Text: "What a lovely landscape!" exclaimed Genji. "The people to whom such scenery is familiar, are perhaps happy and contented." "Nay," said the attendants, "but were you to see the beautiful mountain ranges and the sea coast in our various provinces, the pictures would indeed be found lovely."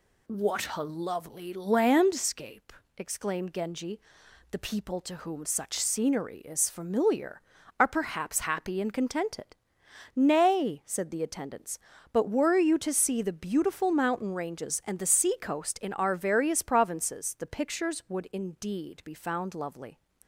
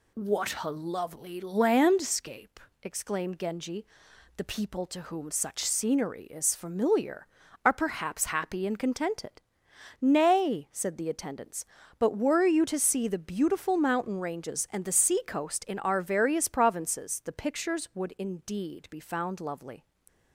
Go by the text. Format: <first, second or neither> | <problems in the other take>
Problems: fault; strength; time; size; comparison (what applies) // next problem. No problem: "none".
neither | none